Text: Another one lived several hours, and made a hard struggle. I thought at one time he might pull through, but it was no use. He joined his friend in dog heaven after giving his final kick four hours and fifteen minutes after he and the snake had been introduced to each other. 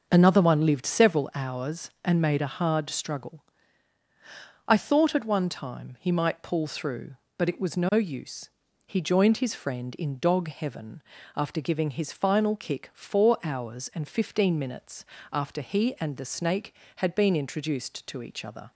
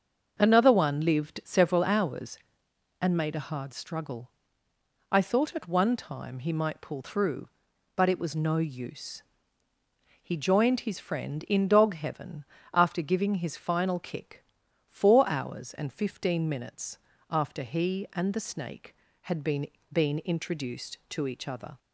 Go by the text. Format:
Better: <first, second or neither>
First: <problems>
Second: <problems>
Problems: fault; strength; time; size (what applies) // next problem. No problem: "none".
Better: first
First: starts louder than the rest; until 1.1 s; 6.5 dB // pauses between "heaven" and "after"; slight; at 11.0 s; 0.36 s long // pauses between "minutes" and "after"; slight; at 15.0 s; 0.26 s long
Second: starts louder than the rest; until 1.4 s; 6.5 dB // pauses between "heaven" and "after"; slight; at 12.4 s; 0.30 s long // pauses between "kick" and "four"; noticeable; at 14.4 s; 0.46 s long // pauses between "minutes" and "after"; slight; at 16.9 s; 0.32 s long // says "been" twice; at 19.9 s